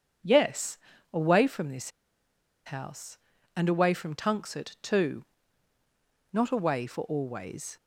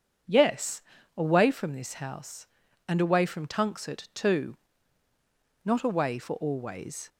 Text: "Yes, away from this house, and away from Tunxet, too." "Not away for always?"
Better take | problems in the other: second | pauses between "this" and "house"; noticeable; at 1.9 s; 0.75 s long

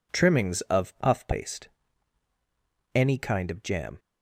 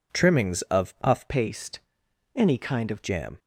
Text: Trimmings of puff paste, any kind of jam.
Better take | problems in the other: first | changes voice from "paste" to "of"; from 1.2 to 3.0 s; 1.8 s long

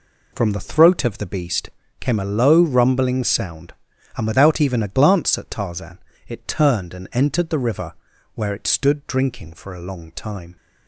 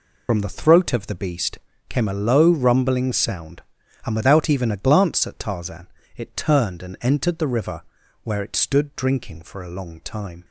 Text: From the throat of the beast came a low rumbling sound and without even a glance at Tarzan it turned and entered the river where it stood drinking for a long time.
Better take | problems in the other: first | loses the start of "From"; at 0.2 s; 70 ms // pauses between "beast" and "came"; slight; at 1.5 s; 0.30 s long; slight in the first // pauses between "Tarzan" and "it"; slight; at 5.8 s; 0.28 s long; slight in the first // pauses between "river" and "where"; at 7.8 s; 0.40 s long; also in the first

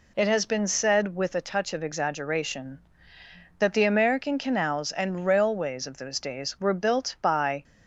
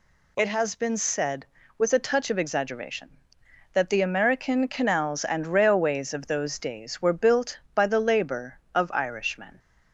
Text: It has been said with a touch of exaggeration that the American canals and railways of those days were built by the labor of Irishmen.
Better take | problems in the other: second | stops before "the labor of Irishmen"; at 7.6 s

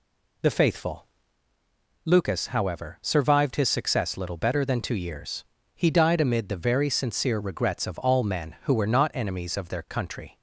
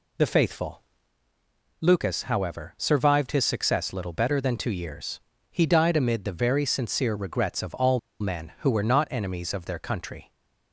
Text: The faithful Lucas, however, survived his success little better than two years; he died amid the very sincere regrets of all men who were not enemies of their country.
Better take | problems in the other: first | pauses between "faithful" and "Lucas"; noticeable; at 0.8 s; 0.98 s long; noticeable in the first // pauses between "all" and "men"; slight; at 7.9 s; 0.22 s long

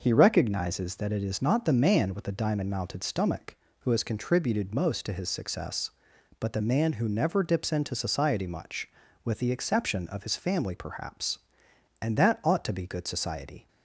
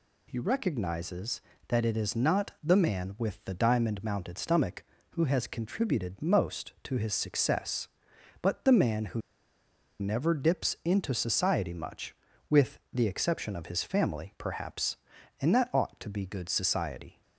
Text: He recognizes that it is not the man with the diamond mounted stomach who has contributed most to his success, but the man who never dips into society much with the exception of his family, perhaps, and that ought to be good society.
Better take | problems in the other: first | pauses between "who" and "never"; noticeable; at 9.2 s; 0.80 s long

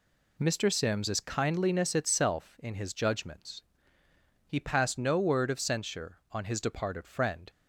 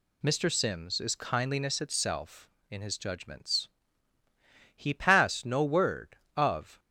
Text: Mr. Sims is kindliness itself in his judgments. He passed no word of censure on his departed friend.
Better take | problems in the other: first | stops before "censure on his departed friend"; at 6.7 s

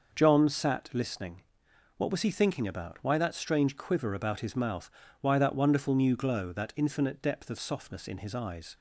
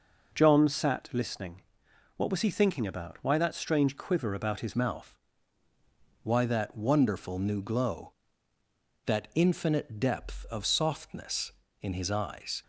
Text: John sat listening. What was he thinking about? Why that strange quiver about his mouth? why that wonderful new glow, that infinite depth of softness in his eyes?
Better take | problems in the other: first | changes voice at "mouth"; from 4.7 s on; 7.9 s long

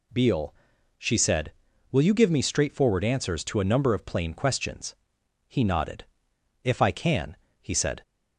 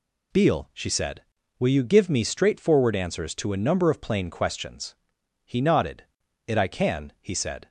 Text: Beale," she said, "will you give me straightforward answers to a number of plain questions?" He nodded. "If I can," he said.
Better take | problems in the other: first | says "It" for "If"; at 6.4 s

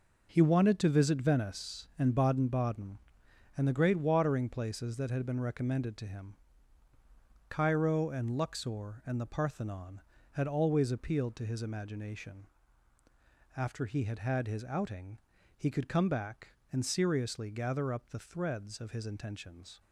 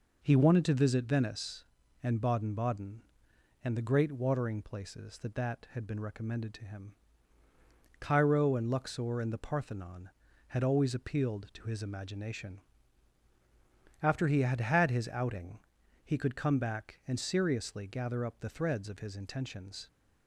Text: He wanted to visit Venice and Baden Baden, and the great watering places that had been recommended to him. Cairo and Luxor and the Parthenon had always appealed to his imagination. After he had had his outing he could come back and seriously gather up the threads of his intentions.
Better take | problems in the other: first | says "that" twice; at 5.3 s // pauses between "outing" and "he"; noticeable; at 15.5 s; 0.46 s long; also in the first

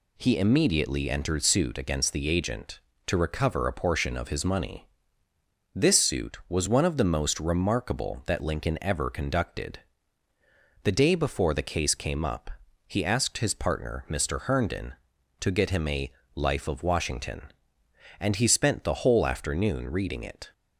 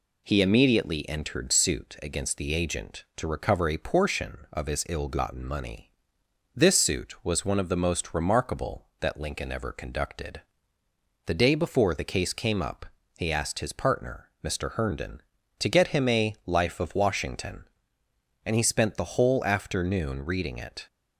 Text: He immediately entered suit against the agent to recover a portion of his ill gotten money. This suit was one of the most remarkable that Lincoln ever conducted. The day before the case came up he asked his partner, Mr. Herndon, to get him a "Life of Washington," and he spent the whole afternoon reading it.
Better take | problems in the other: second | skips "ill gotten"; at 4.4 s // pauses between "up" and "he"; at 12.5 s; 0.38 s long; slight in the second // pauses between "a" and "Life"; slight; at 16.1 s; 0.24 s long

